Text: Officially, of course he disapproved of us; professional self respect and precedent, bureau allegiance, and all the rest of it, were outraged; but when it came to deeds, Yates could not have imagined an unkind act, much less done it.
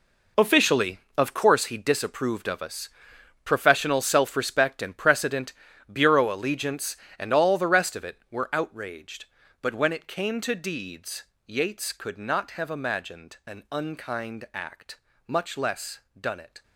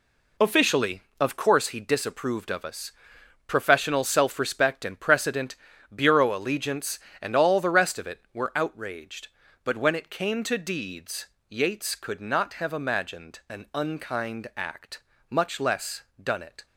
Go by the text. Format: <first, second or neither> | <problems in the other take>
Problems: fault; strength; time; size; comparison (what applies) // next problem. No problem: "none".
second | gets quieter; strong; throughout; 12.5 dB // pauses between "less" and "done"; slight; at 16.0 s; 0.18 s long; slight in the second